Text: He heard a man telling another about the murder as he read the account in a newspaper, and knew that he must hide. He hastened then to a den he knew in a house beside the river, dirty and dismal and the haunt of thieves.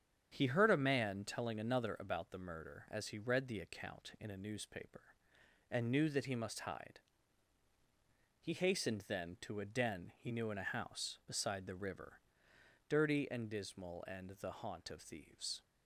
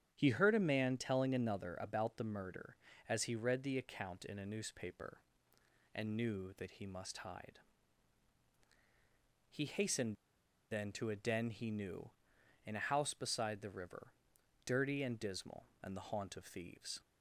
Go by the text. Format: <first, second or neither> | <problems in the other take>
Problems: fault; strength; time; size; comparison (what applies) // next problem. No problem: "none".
first | starts louder than the rest; strong; until 1.1 s; 8.5 dB; strong in the first // pauses between "hastened" and "then"; noticeable; at 10.1 s; 0.57 s long